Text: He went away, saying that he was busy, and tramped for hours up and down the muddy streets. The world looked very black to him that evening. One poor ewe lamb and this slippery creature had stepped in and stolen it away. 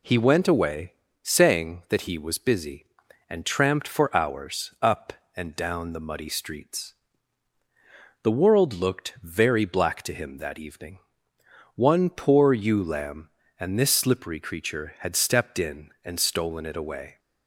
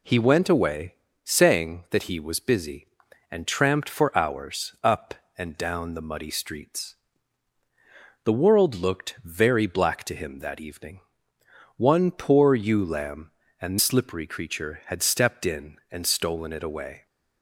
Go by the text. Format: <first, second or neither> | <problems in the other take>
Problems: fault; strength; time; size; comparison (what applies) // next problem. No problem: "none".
first | skips "this"; at 13.7 s